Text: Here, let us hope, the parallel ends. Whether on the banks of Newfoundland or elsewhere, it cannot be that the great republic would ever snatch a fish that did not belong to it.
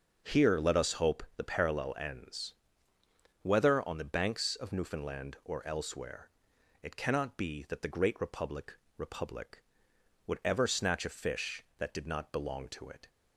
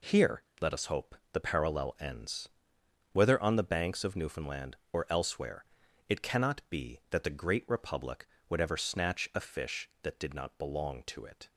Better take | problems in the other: second | starts louder than the rest; noticeable; until 1.4 s; 6 dB // says "republic" twice; at 8.9 s

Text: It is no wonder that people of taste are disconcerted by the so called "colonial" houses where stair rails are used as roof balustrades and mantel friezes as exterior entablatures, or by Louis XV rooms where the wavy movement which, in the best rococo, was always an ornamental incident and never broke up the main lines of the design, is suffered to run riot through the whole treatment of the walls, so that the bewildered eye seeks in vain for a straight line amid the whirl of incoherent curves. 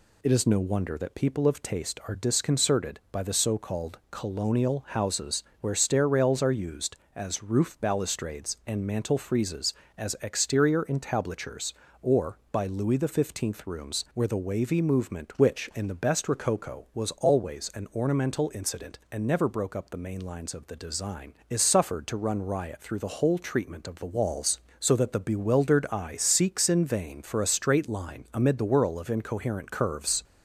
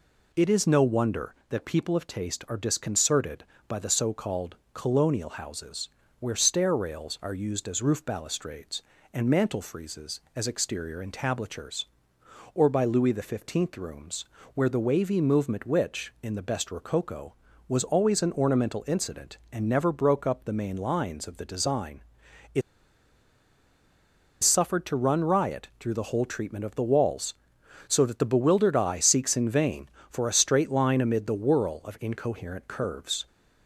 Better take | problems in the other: first | pauses between "called" and "colonial"; slight; at 4.5 s; 0.16 s long // pauses between "houses" and "where"; slight; at 5.8 s; 0.30 s long; slight in the first // pauses between "rooms" and "where"; slight; at 14.2 s; 0.30 s long // pauses between "is" and "suffered"; strong; at 22.6 s; 1.8 s long

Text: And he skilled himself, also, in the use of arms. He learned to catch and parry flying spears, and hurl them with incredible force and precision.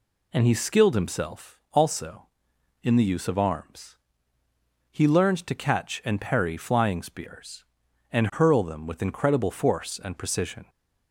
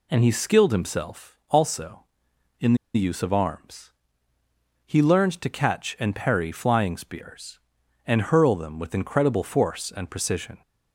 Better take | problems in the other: first | pauses between "in" and "the"; slight; at 2.7 s; 0.20 s long

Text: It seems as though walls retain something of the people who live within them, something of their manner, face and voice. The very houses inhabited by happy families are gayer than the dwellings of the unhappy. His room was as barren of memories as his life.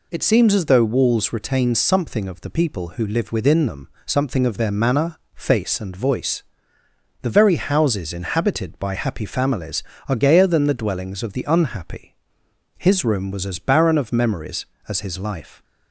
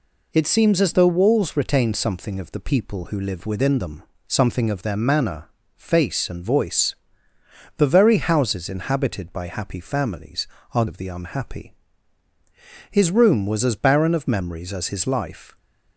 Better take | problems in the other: first | skips "gayer than the dwellings"; at 10.8 s

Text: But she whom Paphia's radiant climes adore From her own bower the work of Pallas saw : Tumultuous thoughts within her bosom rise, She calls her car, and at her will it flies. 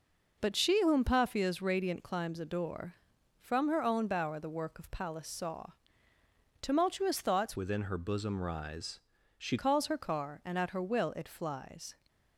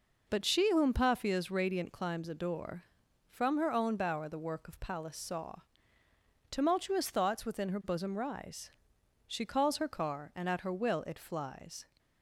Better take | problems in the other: second | changes voice from "within" to "She"; from 7.5 to 9.5 s; 2.0 s long

